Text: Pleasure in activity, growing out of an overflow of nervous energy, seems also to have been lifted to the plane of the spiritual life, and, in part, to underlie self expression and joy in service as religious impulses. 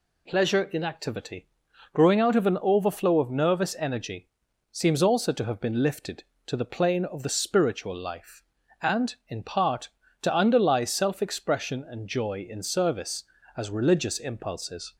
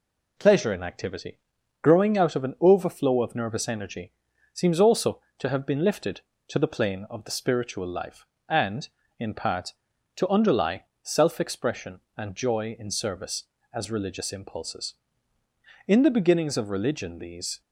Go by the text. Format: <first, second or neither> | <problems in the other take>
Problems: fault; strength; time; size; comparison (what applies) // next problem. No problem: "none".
first | pauses between "underlie" and "self"; slight; at 10.8 s; 0.18 s long // goes on to say "In the beginnings of religion these"; strong; from 15.8 s on; 1.7 s long